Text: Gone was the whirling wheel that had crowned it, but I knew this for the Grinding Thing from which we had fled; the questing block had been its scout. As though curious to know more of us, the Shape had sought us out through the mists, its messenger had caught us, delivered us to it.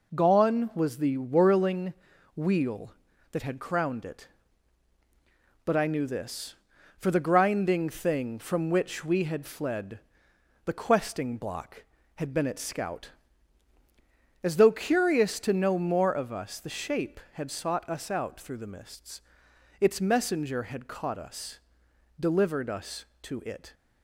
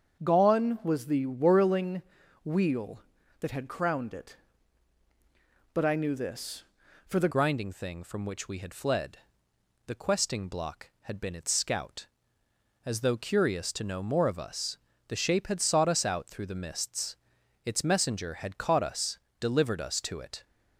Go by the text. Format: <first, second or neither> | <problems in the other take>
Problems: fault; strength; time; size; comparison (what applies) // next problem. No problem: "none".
first | starts louder than the rest; until 1.2 s; 6.5 dB // pauses between "whirling" and "wheel"; at 2.0 s; 0.44 s long; also in the first // changes voice at "Grinding"; from 7.3 s on; 13.1 s long